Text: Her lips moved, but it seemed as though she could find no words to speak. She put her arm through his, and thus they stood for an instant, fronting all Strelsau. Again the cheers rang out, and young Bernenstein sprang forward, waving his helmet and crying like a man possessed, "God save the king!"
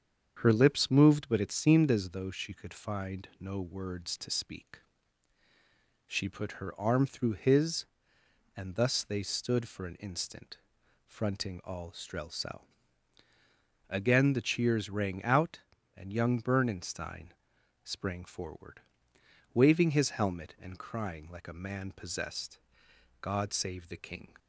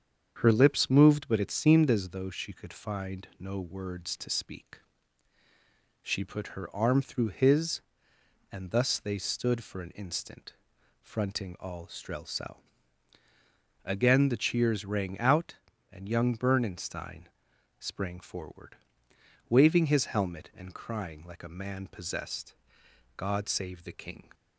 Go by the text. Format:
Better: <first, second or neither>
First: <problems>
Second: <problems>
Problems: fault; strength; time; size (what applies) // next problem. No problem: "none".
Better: neither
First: starts louder than the rest; strong; until 1.4 s; 7.5 dB // pauses between "Bernenstein" and "sprang"; noticeable; at 17.3 s; 0.50 s long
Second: starts louder than the rest; strong; until 1.4 s; 7.5 dB // pauses between "Bernenstein" and "sprang"; noticeable; at 17.2 s; 0.50 s long